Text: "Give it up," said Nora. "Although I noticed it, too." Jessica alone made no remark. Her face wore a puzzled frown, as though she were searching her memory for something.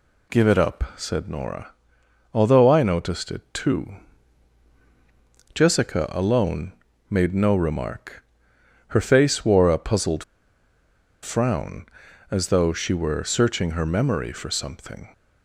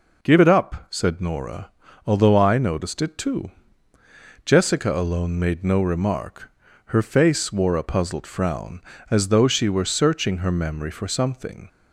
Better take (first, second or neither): second